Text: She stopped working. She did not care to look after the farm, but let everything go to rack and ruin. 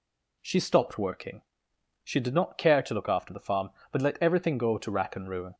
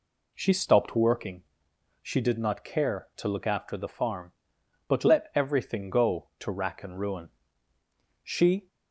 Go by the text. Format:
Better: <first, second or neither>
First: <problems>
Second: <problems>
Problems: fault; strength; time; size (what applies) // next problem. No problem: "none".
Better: first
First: none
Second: goes on to say "She"; slight; from 8.2 s on; 0.44 s long